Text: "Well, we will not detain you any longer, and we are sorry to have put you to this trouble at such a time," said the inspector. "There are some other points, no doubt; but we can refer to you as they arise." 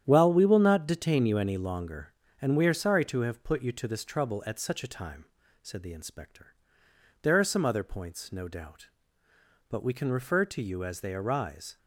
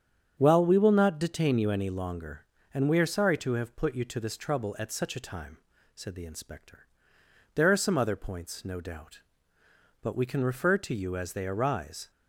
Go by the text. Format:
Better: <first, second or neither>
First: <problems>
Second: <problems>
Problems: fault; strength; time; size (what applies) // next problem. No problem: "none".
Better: second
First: gets quieter; strong; throughout; 9 dB // starts louder than the rest; strong; until 1.0 s; 9.5 dB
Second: starts louder than the rest; strong; until 1.4 s; 8.5 dB